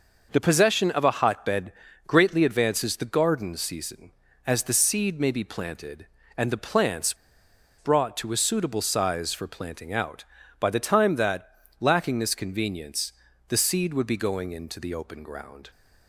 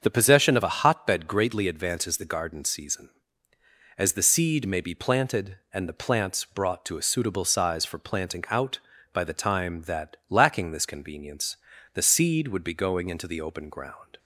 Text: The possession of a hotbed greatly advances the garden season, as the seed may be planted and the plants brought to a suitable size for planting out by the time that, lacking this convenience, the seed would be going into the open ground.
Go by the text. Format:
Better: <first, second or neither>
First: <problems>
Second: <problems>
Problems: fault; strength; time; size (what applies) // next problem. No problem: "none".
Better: second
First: starts louder than the rest; noticeable; until 1.3 s; 6 dB // pauses between "hotbed" and "greatly"; slight; at 1.7 s; 0.34 s long // pauses between "plants" and "brought"; noticeable; at 7.1 s; 0.63 s long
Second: starts louder than the rest; until 1.0 s; 7 dB